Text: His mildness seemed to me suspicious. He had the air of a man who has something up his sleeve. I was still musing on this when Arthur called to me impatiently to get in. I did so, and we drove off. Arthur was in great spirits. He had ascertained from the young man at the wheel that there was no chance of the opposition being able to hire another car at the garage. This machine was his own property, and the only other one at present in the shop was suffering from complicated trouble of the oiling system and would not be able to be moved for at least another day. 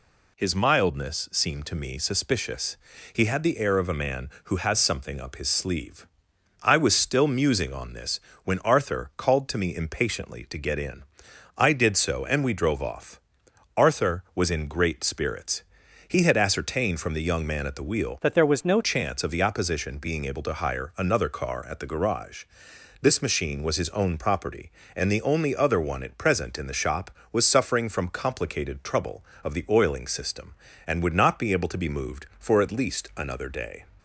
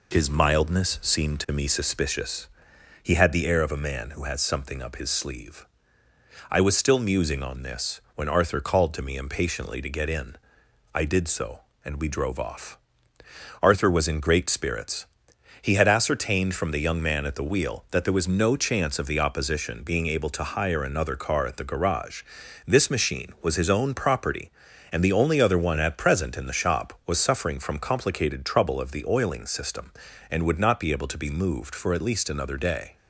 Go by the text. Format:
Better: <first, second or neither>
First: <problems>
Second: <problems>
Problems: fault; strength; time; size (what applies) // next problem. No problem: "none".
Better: second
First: pauses between "this" and "when"; slight; at 8.1 s; 0.24 s long // changes voice from "that" to "no"; from 18.2 to 18.8 s; 0.6 s long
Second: pauses between "this" and "when"; slight; at 7.9 s; 0.16 s long